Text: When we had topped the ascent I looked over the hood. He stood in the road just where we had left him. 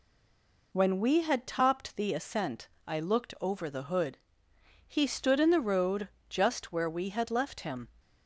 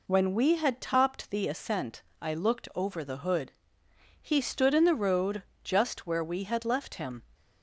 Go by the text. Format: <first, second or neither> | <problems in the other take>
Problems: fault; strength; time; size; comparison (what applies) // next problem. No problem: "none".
second | stays silent before the first word; slight; until 0.7 s; 0.7 s long // pauses between "ascent" and "I"; slight; at 2.6 s; 0.18 s long; slight in the second // pauses between "road" and "just"; slight; at 6.0 s; 0.22 s long; slight in the second